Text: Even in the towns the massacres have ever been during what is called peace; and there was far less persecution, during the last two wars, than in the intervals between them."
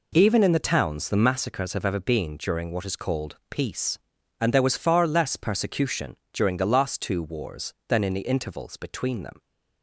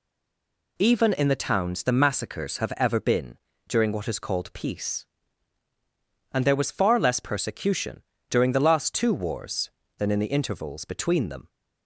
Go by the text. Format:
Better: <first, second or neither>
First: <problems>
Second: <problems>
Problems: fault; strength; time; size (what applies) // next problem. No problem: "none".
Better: first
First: none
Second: stays silent before the first word; slight; until 0.7 s; 0.7 s long // pauses between "been" and "during"; slight; at 3.3 s; 0.28 s long